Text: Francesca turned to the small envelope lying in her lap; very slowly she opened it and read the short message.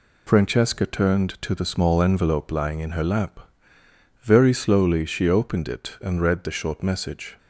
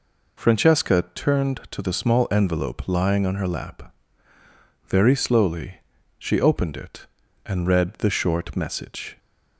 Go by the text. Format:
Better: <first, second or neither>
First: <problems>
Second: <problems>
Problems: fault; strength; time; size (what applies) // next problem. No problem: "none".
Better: first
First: none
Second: says "on" for "in"; at 3.2 s // pauses between "slowly" and "she"; slight; at 5.8 s; 0.36 s long